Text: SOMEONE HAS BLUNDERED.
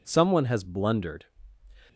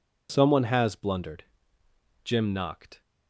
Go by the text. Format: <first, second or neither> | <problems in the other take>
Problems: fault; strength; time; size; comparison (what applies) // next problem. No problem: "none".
first | goes on to say "Jim knocked"; noticeable; from 2.2 s on; 0.78 s long